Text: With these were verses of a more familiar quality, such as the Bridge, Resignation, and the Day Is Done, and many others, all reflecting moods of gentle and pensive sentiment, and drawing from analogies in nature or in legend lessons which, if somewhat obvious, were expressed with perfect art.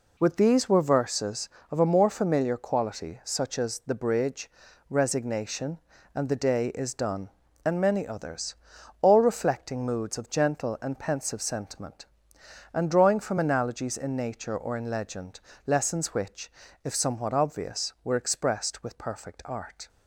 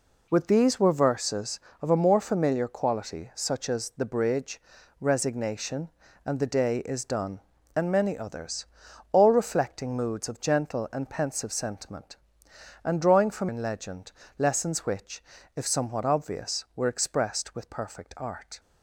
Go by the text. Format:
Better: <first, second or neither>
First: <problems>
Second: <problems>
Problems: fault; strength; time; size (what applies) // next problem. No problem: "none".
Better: first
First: pauses between "legend" and "lessons"; slight; at 15.4 s; 0.26 s long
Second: skips "analogies in nature or"; at 13.4 s // pauses between "legend" and "lessons"; slight; at 14.1 s; 0.26 s long